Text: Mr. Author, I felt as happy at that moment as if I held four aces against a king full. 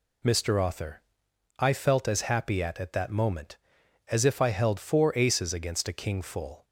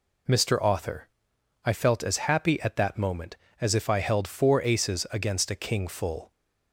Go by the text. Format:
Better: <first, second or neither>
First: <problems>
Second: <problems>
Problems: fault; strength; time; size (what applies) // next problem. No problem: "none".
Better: second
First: says "at" twice; at 2.7 s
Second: none